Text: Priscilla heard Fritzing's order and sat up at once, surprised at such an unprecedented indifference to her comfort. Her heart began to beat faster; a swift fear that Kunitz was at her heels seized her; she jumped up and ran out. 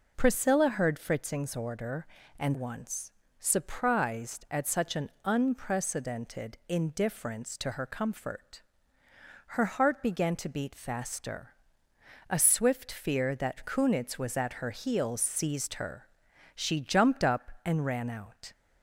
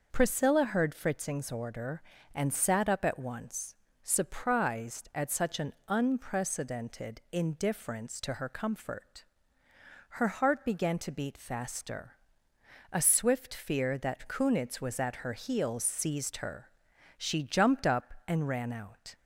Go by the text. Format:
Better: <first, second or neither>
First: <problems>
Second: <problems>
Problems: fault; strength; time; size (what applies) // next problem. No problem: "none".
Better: second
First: skips "sat up at"; at 2.5 s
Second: none